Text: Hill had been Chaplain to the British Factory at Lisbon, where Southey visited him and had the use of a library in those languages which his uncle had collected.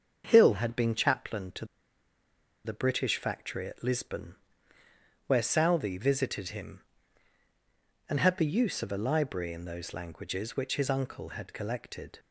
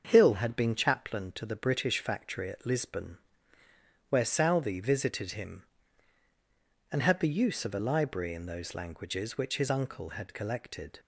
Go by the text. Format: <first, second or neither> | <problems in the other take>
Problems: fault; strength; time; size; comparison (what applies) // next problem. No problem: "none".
second | starts louder than the rest; until 1.2 s; 6.5 dB; also in the second // pauses between "to" and "the"; at 1.6 s; 0.99 s long